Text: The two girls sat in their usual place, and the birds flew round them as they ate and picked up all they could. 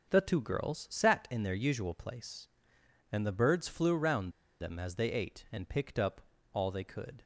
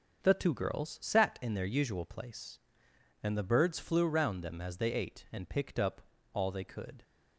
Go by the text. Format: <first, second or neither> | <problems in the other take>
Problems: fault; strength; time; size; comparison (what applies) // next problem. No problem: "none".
second | starts louder than the rest; until 1.1 s; 6 dB; also in the second // pauses between "round" and "them"; slight; at 4.3 s; 0.29 s long // pauses between "up" and "all"; slight; at 6.2 s; 0.32 s long; slight in the second